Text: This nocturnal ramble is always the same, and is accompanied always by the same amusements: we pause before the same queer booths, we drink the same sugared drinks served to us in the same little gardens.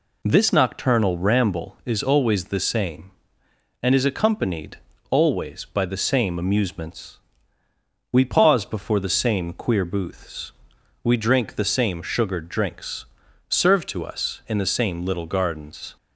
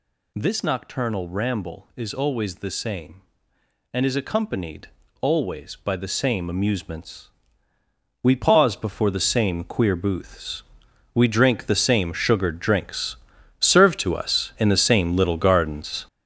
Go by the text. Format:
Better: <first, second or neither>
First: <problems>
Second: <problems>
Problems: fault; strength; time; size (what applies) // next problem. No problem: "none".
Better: first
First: pauses between "accompanied" and "always"; slight; at 4.7 s; 0.34 s long // pauses between "drinks" and "served"; at 13.0 s; 0.42 s long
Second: gets louder; strong; throughout; 8 dB // pauses between "accompanied" and "always"; slight; at 4.8 s; 0.34 s long // pauses between "drinks" and "served"; at 13.1 s; 0.42 s long